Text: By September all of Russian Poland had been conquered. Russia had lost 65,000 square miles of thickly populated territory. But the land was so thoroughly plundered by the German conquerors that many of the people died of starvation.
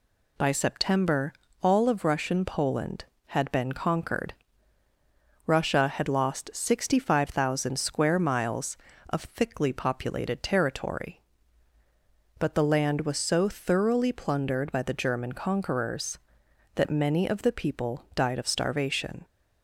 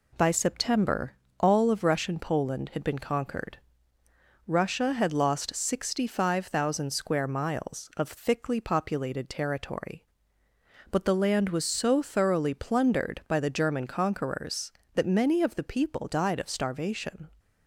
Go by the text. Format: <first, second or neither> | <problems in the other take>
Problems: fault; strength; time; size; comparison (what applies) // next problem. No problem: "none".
neither | pauses between "September" and "all"; slight; the same in both